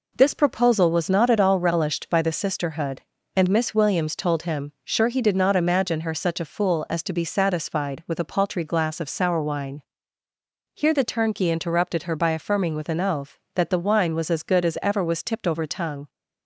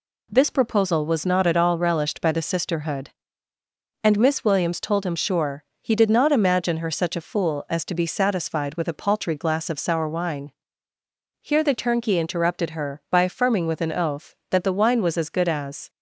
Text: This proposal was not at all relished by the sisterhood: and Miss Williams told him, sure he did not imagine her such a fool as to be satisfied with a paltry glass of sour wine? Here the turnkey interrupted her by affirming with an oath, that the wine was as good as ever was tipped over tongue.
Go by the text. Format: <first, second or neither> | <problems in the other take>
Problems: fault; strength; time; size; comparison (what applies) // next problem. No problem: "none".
first | pauses between "sure" and "he"; slight; at 5.6 s; 0.18 s long // stops before "ever was tipped over tongue"; at 15.8 s